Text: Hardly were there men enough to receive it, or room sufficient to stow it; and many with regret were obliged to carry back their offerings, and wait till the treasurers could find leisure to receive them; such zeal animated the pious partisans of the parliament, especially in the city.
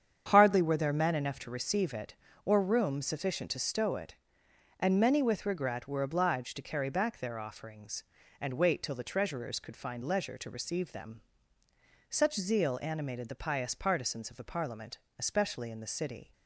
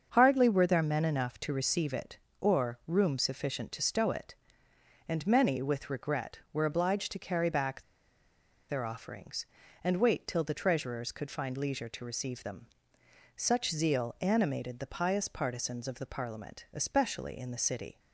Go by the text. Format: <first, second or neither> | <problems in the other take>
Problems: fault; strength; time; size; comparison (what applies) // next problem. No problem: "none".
first | starts louder than the rest; until 1.1 s; 7 dB; strong in the first // pauses between "back" and "their"; noticeable; at 7.8 s; 0.86 s long